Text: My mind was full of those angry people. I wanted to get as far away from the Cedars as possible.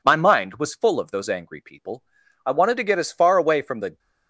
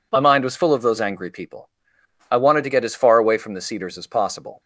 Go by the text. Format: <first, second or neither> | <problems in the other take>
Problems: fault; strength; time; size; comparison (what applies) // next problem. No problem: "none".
second | stops before "Cedars as possible"; at 3.9 s